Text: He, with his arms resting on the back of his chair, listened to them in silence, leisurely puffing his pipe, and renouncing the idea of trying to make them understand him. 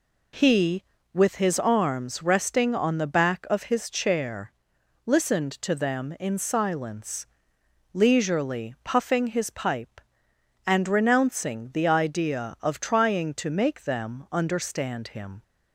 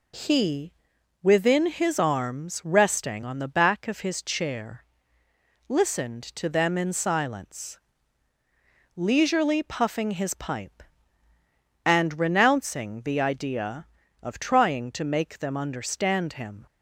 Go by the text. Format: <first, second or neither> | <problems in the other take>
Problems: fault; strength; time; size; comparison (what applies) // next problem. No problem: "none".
first | says "within" for "with"; at 1.2 s